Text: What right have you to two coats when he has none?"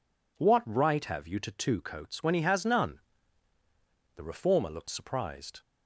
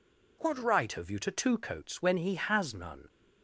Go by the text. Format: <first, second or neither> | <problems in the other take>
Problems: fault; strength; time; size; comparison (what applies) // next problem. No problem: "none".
second | goes on to say "The reformer looked surprised"; from 4.1 s on; 1.4 s long